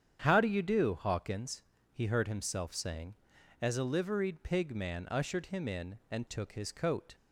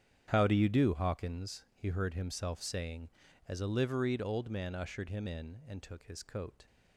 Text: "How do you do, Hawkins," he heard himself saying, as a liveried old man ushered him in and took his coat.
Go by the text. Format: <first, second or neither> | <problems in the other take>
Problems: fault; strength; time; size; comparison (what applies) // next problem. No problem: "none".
second | starts louder than the rest; strong; until 1.2 s; 8.5 dB; strong in the second // says "pig" for "old"; at 4.4 s